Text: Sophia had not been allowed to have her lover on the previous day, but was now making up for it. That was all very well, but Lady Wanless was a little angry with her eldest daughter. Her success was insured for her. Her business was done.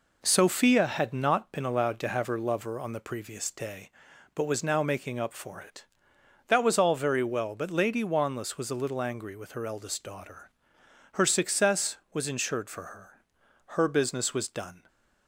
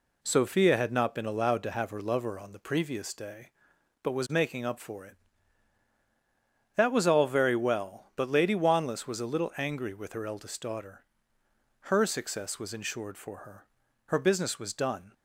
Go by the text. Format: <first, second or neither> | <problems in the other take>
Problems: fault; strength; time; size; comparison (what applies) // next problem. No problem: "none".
first | skips "now"; at 4.2 s